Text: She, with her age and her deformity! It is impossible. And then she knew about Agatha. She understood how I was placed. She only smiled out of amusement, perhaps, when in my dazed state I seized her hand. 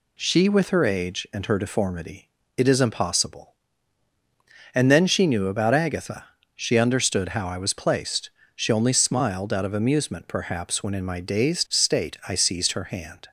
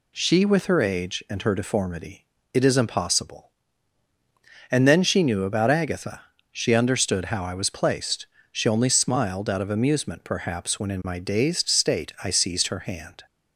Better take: neither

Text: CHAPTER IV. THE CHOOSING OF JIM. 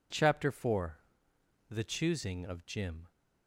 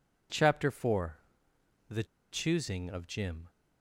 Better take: first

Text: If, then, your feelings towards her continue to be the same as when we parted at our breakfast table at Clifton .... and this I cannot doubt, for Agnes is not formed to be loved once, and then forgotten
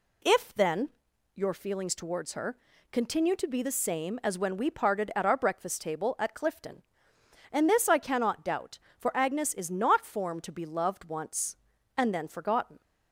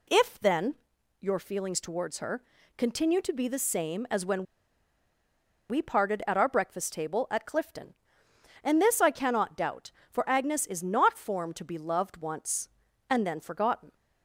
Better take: first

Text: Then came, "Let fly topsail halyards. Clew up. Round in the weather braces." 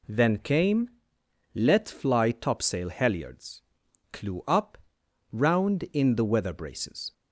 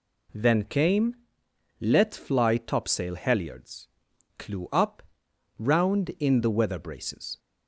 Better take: neither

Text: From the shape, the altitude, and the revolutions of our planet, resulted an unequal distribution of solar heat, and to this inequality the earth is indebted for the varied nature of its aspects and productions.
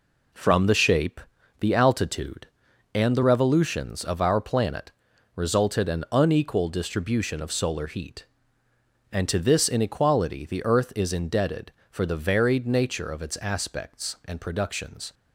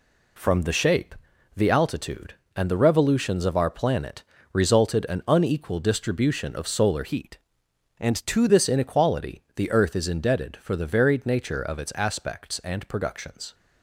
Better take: first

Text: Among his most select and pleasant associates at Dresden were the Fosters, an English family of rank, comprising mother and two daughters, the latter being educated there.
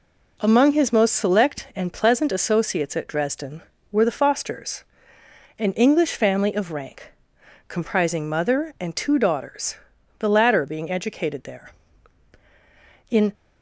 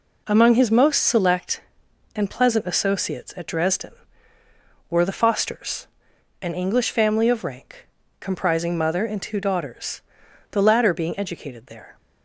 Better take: second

